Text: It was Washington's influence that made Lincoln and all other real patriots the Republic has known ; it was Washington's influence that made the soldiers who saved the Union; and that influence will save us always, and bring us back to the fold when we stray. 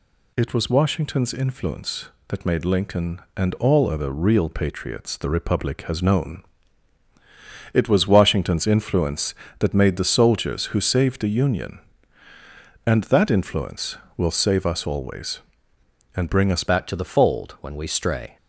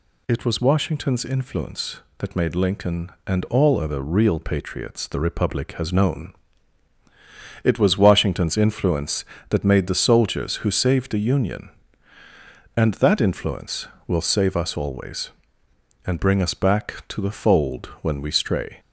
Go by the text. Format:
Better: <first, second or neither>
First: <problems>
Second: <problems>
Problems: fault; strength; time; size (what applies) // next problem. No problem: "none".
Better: second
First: changes voice at "back"; from 16.6 s on; 1.7 s long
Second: none